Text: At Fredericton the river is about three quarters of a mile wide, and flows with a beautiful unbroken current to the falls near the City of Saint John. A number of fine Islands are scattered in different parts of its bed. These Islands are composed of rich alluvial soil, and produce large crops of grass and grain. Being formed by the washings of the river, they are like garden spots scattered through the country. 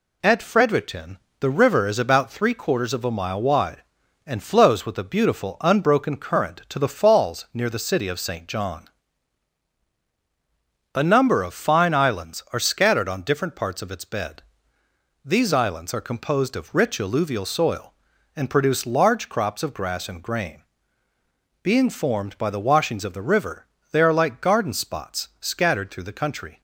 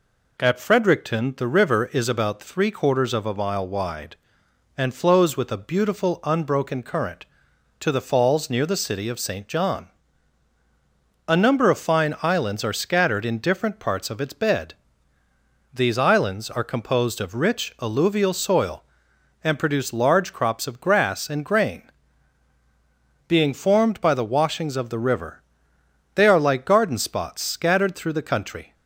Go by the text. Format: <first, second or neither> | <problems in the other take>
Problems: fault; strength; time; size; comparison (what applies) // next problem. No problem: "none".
second | pauses between "Fredericton" and "the"; slight; at 1.1 s; 0.22 s long // says "on" for "in"; at 13.0 s